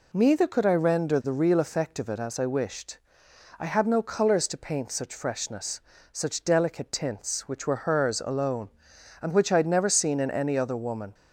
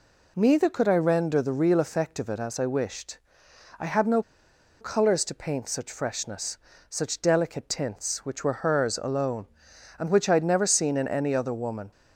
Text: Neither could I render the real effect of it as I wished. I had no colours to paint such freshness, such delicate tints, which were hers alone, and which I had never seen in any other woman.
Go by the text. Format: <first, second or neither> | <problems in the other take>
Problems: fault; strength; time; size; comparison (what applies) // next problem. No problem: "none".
first | pauses between "no" and "colours"; noticeable; at 4.2 s; 0.58 s long